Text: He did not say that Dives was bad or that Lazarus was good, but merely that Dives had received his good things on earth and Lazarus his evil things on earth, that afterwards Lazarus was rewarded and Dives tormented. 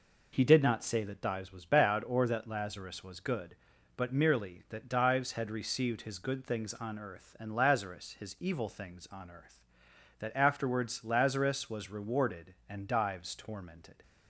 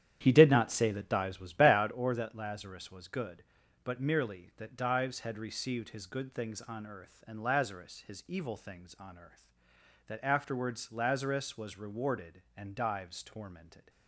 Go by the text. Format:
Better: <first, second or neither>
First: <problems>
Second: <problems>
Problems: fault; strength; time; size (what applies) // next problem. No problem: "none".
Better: first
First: none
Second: starts louder than the rest; strong; until 2.0 s; 10 dB